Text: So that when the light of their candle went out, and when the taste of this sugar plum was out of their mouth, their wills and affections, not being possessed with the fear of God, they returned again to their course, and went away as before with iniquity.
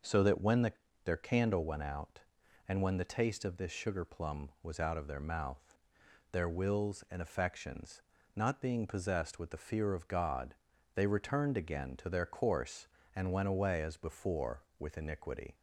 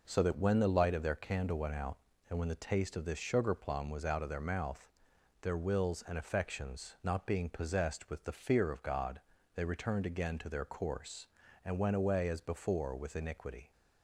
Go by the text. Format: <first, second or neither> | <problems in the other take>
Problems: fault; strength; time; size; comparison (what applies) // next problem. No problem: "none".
second | skips "light of"; at 0.8 s